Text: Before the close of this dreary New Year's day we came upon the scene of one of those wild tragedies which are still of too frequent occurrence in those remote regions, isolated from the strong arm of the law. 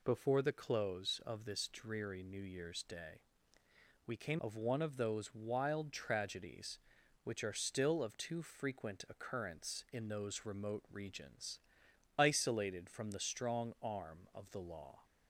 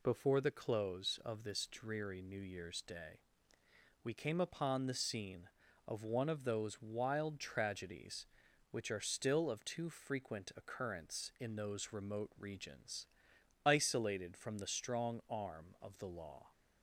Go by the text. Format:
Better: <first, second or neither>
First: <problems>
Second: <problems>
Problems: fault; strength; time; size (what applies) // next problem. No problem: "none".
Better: second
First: pauses between "day" and "we"; noticeable; at 3.2 s; 0.84 s long // skips "upon the scene"; at 4.3 s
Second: pauses between "day" and "we"; noticeable; at 3.1 s; 0.82 s long